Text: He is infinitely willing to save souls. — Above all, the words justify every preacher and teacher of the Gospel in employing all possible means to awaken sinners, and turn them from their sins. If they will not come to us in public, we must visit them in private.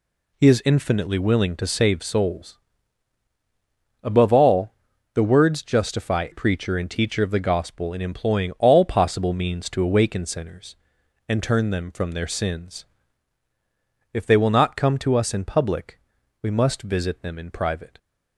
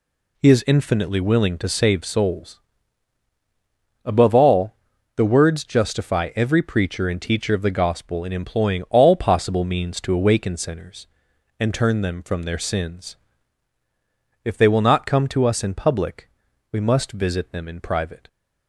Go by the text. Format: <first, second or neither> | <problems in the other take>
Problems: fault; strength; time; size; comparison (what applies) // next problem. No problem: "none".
second | skips "every"; at 6.3 s